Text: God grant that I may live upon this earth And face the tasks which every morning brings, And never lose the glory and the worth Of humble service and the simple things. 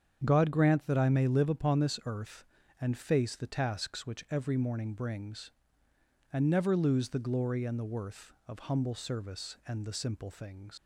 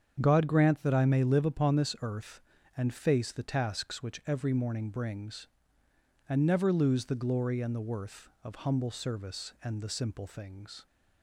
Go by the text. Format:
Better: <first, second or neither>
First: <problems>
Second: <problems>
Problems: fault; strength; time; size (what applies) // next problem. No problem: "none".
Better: second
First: starts louder than the rest; strong; until 1.2 s; 8 dB // leaves "things" unfinished; at 10.7 s; 125 ms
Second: starts louder than the rest; strong; until 1.2 s; 8 dB